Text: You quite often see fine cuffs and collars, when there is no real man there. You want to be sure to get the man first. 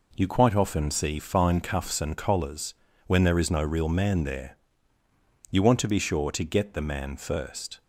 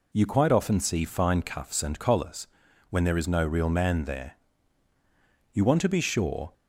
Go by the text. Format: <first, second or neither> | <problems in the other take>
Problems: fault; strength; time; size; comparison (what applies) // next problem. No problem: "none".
first | stops before "to get the man first"; at 6.5 s